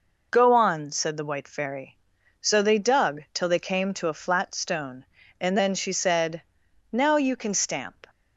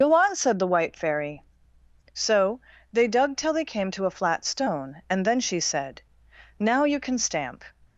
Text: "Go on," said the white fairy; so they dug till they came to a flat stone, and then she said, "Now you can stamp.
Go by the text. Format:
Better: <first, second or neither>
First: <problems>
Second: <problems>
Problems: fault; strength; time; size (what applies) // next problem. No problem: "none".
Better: first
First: none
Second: loses the start of "Go"; at 0.0 s; 95 ms // pauses between "so" and "they"; slight; at 2.5 s; 0.32 s long